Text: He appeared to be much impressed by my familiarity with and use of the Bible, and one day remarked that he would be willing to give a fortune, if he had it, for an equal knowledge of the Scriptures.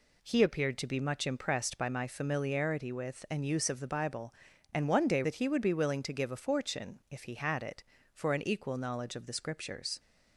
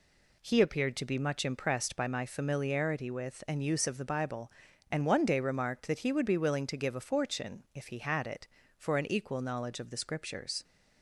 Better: second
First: skips "remarked"; at 5.2 s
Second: none

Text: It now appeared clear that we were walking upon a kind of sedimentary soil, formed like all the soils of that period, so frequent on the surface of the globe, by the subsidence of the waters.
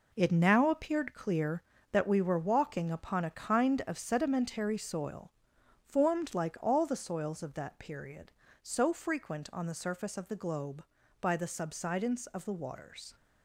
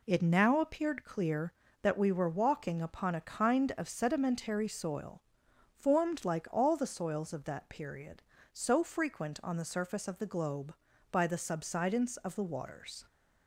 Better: second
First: gets quieter; strong; throughout; 8 dB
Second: none

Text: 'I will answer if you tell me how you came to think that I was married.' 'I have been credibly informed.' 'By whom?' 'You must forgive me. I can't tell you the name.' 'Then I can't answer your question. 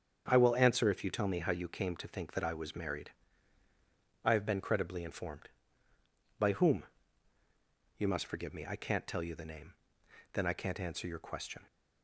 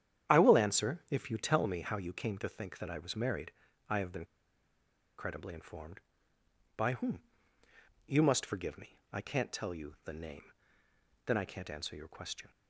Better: first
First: starts louder than the rest; strong; until 1.3 s; 7.5 dB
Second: starts louder than the rest; strong; until 1.3 s; 10 dB // pauses between "been" and "credibly"; noticeable; at 4.2 s; 0.94 s long

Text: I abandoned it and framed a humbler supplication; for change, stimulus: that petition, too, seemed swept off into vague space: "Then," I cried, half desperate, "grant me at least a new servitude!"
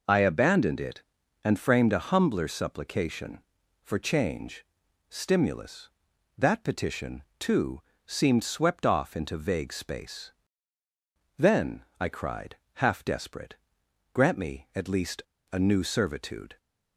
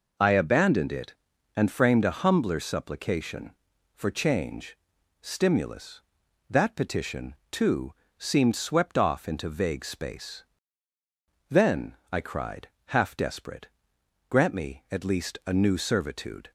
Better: second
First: pauses between "least" and "a"; slight; at 15.2 s; 0.30 s long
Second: none

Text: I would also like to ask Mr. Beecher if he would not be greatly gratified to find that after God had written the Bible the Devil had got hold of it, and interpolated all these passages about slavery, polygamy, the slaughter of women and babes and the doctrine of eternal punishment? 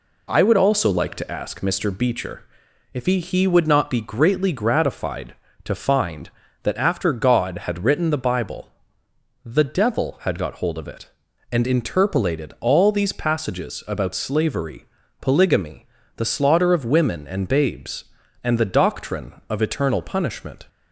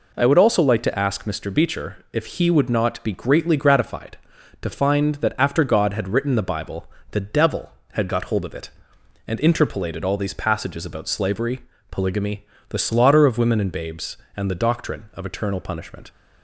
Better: second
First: pauses between "Beecher" and "if"; noticeable; at 2.4 s; 0.50 s long // says "he" twice; at 3.1 s // pauses between "Bible" and "the"; noticeable; at 8.6 s; 0.74 s long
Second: pauses between "Bible" and "the"; slight; at 6.8 s; 0.26 s long

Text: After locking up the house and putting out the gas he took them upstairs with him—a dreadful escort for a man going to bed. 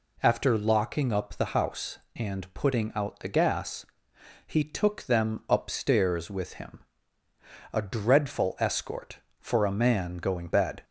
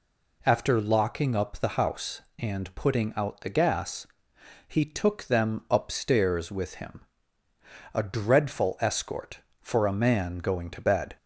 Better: second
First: pauses between "gas" and "he"; noticeable; at 3.8 s; 0.60 s long // skips "to"; at 10.4 s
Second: pauses between "gas" and "he"; noticeable; at 4.0 s; 0.60 s long

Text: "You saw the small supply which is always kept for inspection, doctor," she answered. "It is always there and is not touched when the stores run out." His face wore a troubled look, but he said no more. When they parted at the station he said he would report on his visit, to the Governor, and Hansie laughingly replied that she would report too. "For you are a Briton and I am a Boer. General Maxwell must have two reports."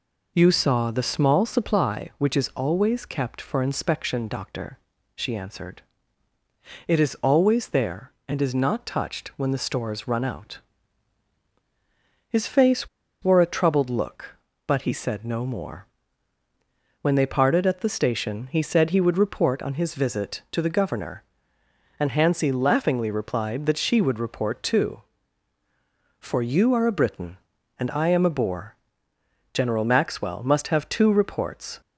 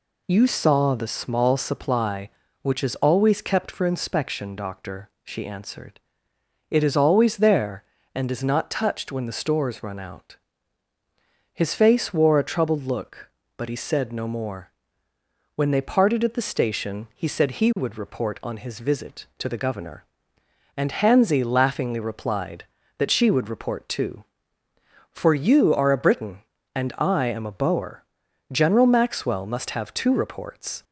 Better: second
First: pauses between "face" and "wore"; slight; at 12.8 s; 0.34 s long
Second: none

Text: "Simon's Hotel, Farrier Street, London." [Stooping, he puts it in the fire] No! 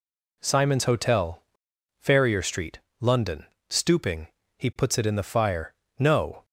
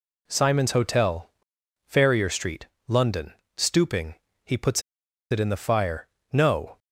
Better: first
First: pauses between "fire" and "No"; slight; at 5.7 s; 0.24 s long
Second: pauses between "puts" and "it"; noticeable; at 4.8 s; 0.49 s long // pauses between "fire" and "No"; slight; at 6.0 s; 0.24 s long

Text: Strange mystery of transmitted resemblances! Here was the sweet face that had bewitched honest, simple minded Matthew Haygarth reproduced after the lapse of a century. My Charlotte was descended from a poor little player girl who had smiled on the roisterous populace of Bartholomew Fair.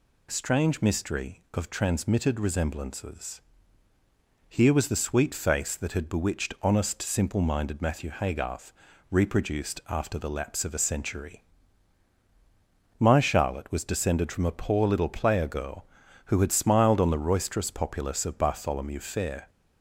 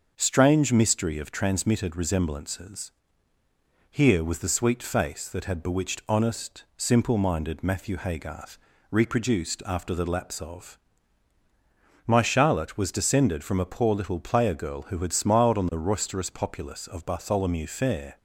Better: first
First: pauses between "Haygarth" and "reproduced"; at 8.7 s; 0.38 s long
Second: starts louder than the rest; until 1.1 s; 6.5 dB // pauses between "Haygarth" and "reproduced"; slight; at 8.5 s; 0.34 s long // skips "a century"; at 11.4 s

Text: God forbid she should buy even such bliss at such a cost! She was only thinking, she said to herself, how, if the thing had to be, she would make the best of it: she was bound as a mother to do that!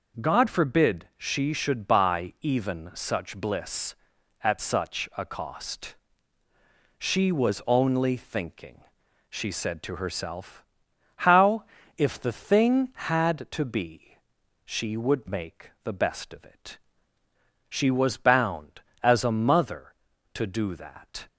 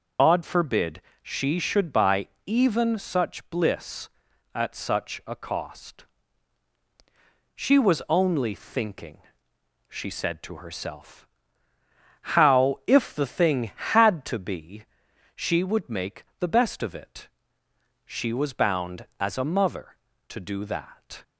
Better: first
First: none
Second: loses the start of "God"; at 0.1 s; 90 ms // pauses between "forbid" and "she"; slight; at 1.0 s; 0.22 s long // pauses between "buy" and "even"; slight; at 2.2 s; 0.18 s long // pauses between "make" and "the"; slight; at 16.2 s; 0.16 s long

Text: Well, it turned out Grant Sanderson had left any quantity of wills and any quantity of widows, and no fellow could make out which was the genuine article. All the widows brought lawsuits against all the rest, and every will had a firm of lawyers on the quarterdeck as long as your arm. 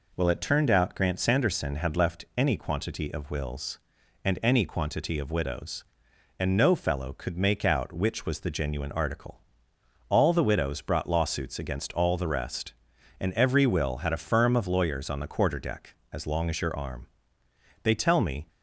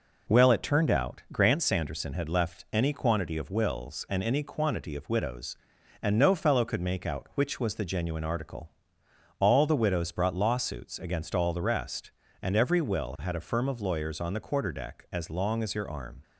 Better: second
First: goes on to say "They tell me"; noticeable; from 17.8 s on; 0.64 s long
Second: none

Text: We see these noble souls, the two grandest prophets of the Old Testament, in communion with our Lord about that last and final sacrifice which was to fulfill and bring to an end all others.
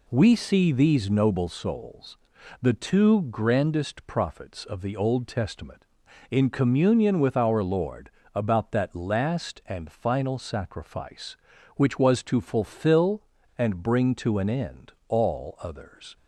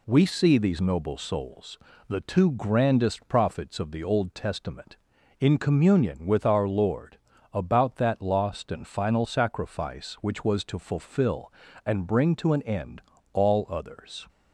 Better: first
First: pauses between "Lord" and "about"; slight; at 8.0 s; 0.24 s long // pauses between "end" and "all"; slight; at 14.9 s; 0.16 s long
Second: pauses between "Lord" and "about"; slight; at 7.1 s; 0.34 s long // says "lost" for "last"; at 8.1 s // pauses between "end" and "all"; slight; at 13.0 s; 0.30 s long

